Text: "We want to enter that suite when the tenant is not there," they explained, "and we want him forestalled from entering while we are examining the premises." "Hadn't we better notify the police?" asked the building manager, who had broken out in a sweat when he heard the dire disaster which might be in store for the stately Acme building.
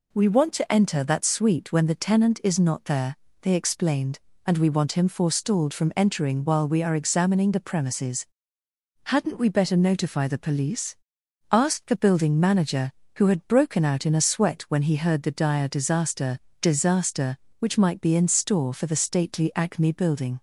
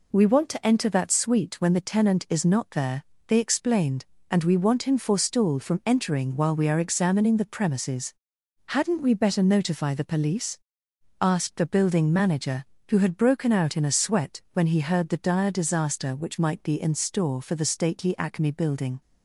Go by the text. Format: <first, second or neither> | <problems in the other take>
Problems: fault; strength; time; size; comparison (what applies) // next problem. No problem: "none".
second | says "disaster" twice; at 16.6 s